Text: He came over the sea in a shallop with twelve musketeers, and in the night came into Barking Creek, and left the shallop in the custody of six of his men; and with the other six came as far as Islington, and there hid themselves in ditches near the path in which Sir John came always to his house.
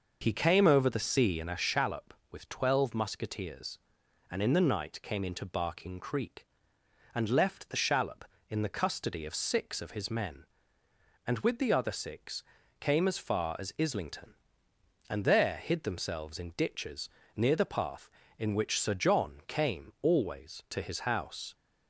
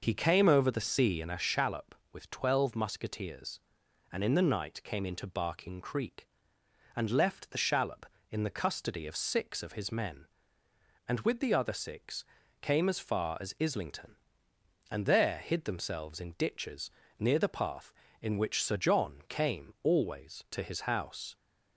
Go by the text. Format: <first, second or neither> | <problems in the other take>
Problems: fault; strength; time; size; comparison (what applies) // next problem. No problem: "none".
neither | pauses between "six" and "came"; slight; the same in both // pauses between "ditches" and "near"; slight; the same in both